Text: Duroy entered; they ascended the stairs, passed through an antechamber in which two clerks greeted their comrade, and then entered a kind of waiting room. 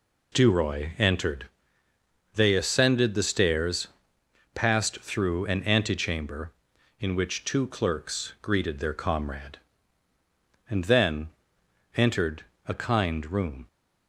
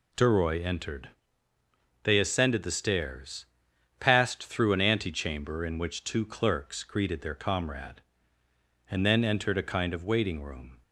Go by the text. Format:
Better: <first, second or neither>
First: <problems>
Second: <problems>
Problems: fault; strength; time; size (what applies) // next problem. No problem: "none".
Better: second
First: pauses between "then" and "entered"; noticeable; at 11.2 s; 0.66 s long // pauses between "entered" and "a"; slight; at 12.4 s; 0.20 s long // skips "of waiting"; at 13.3 s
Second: none